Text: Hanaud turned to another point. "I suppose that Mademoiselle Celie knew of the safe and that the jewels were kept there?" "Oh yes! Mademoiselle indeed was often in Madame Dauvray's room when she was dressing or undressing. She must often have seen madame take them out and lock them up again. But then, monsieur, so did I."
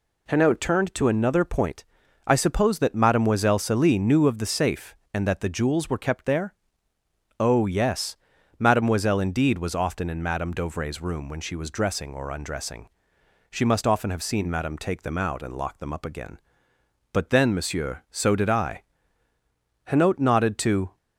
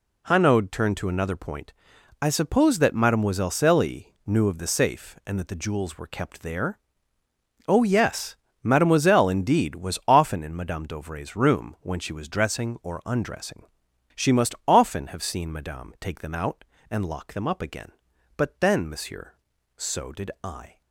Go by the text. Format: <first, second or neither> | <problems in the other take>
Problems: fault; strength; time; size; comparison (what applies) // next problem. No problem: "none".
second | goes on to say "Hanaud nodded to"; noticeable; from 19.8 s on; 1.1 s long